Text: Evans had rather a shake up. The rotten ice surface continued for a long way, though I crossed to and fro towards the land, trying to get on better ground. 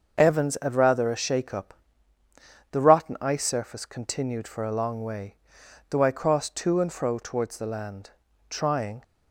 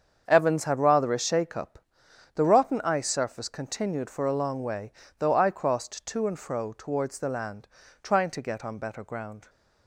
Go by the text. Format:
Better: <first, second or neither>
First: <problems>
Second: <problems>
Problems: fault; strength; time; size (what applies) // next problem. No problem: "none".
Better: second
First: starts louder than the rest; until 1.2 s; 6.5 dB // stops before "to get on better ground"; at 9.0 s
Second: starts louder than the rest; strong; until 1.2 s; 7.5 dB